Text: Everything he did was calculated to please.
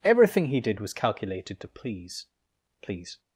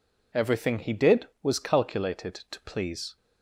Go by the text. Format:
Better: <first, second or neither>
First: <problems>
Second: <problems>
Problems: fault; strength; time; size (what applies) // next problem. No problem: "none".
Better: second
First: says "please" twice; at 2.8 s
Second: none